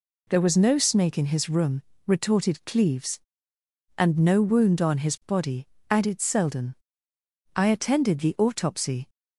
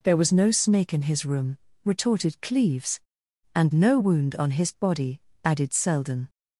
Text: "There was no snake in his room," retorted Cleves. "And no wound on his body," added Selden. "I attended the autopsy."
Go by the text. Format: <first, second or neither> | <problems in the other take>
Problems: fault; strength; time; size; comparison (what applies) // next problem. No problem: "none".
first | stops before "I attended the autopsy"; at 6.2 s